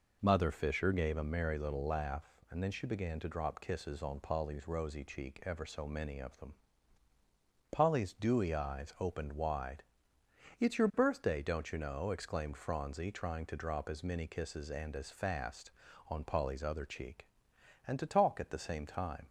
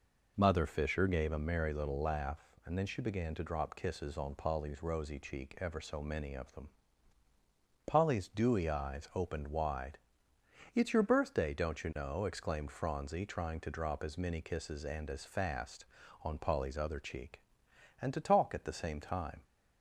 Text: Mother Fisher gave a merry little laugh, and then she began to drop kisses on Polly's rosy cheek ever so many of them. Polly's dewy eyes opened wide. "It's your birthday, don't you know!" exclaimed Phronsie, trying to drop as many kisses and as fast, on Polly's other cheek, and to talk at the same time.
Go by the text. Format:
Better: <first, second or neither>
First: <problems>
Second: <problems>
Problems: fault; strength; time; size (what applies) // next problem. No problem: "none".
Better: neither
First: none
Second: none